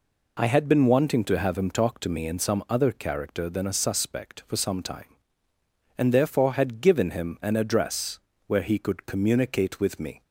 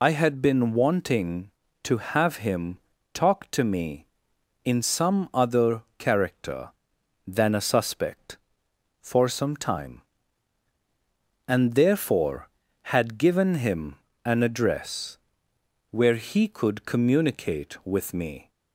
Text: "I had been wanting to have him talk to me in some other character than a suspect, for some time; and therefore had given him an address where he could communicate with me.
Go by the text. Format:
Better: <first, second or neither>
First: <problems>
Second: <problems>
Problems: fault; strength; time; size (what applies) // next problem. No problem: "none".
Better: first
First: pauses between "address" and "where"; slight; at 8.1 s; 0.26 s long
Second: loses the start of "I"; at 0.0 s; 60 ms // pauses between "him" and "talk"; slight; at 2.7 s; 0.34 s long // pauses between "other" and "character"; slight; at 5.8 s; 0.16 s long // pauses between "him" and "an"; slight; at 13.9 s; 0.30 s long // pauses between "address" and "where"; noticeable; at 15.1 s; 0.72 s long